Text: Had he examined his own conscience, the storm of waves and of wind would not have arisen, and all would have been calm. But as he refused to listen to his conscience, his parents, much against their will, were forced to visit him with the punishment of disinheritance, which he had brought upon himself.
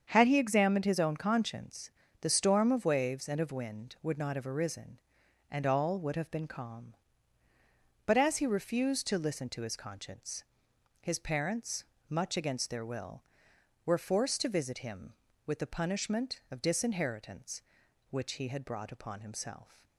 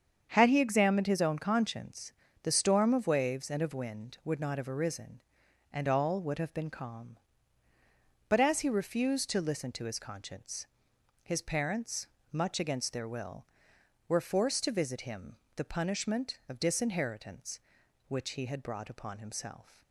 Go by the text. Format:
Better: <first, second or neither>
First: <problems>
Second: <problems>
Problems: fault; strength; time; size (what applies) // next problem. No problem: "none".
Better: first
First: starts louder than the rest; strong; until 1.1 s; 7.5 dB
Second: starts louder than the rest; strong; until 1.3 s; 7.5 dB // skips "with"; at 15.4 s